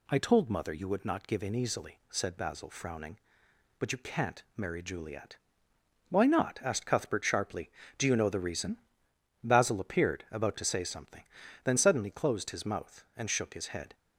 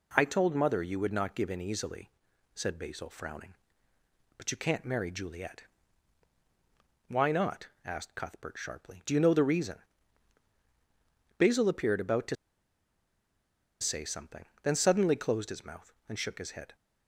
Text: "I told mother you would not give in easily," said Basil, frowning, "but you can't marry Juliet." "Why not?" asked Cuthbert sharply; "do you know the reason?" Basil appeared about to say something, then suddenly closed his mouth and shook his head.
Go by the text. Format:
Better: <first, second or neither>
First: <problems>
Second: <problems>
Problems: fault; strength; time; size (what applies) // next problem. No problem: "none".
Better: first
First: none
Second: pauses between "to" and "say"; strong; at 12.3 s; 1.4 s long